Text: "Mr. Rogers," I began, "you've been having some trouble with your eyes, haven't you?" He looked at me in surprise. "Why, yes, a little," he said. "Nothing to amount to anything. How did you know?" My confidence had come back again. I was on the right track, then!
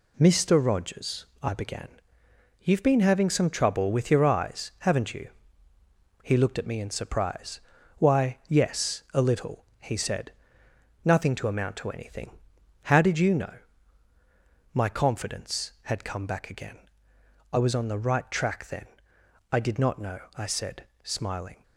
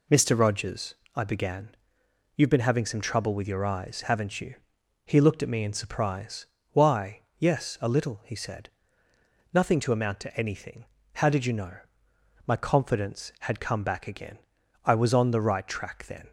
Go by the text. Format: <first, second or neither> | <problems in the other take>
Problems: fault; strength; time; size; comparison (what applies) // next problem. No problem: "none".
second | goes on to say "I did not know I said smiling"; strong; from 19.4 s on; 2.1 s long